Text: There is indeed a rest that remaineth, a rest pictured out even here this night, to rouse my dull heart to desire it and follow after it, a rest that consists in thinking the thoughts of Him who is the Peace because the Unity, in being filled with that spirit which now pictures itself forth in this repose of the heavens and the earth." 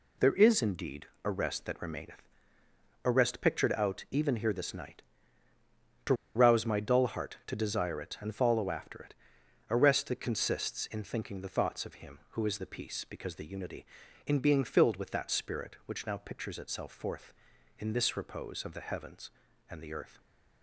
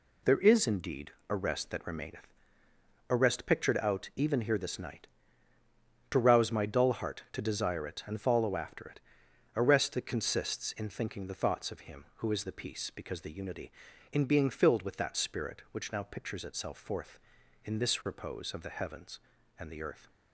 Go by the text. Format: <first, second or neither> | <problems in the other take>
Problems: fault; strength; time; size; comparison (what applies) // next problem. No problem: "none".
second | pauses between "indeed" and "a"; slight; at 1.0 s; 0.18 s long; slight in the second // pauses between "to" and "rouse"; slight; at 6.1 s; 0.22 s long